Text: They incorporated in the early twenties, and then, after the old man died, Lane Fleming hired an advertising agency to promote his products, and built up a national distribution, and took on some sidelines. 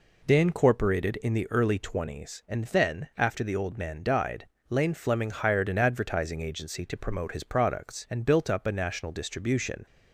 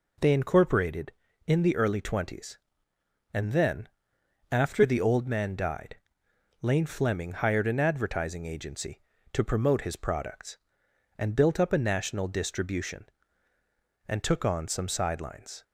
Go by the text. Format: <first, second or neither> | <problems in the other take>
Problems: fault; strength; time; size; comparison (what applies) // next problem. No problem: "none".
second | stops before "and took on some sidelines"; at 9.8 s